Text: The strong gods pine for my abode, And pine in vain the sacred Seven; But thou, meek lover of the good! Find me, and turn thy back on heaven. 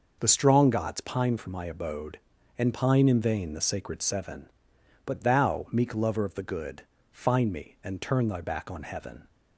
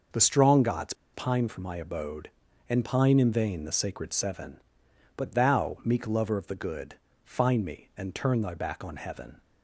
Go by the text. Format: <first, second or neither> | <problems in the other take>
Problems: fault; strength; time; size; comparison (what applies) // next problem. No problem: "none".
first | pauses between "gods" and "pine"; slight; at 0.9 s; 0.20 s long